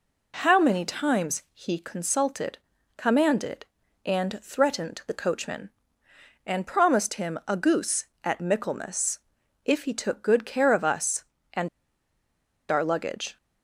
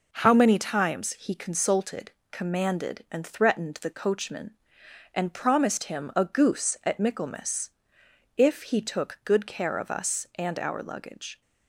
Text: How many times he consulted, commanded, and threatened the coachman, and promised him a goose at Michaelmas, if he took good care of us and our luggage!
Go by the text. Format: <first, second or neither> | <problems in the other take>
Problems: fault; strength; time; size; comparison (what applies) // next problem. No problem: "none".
second | pauses between "and" and "our"; at 11.6 s; 1.0 s long